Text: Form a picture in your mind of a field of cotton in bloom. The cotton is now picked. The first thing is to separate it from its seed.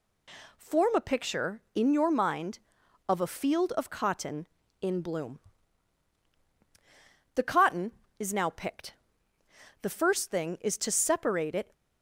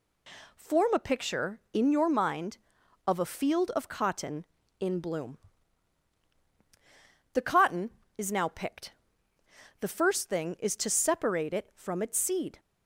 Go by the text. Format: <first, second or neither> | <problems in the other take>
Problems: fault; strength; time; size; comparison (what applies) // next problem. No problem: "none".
second | stops before "from its seed"; at 11.7 s